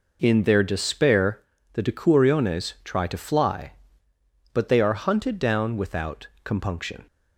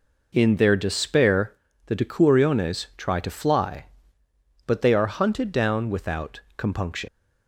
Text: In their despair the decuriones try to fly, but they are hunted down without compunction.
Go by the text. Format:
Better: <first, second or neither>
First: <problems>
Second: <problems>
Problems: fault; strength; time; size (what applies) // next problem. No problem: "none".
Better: first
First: pauses between "despair" and "the"; slight; at 1.4 s; 0.32 s long // pauses between "without" and "compunction"; slight; at 6.2 s; 0.18 s long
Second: pauses between "despair" and "the"; slight; at 1.5 s; 0.32 s long // pauses between "without" and "compunction"; slight; at 6.3 s; 0.18 s long // leaves "compunction" unfinished; at 7.0 s; 110 ms